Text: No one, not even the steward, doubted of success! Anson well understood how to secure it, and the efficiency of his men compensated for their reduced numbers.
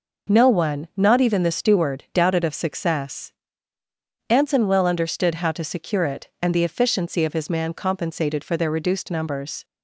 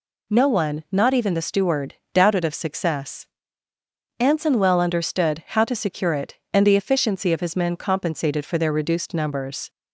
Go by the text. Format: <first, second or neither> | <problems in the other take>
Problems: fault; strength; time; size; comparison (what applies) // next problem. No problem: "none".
second | says "man" for "men"; at 7.4 s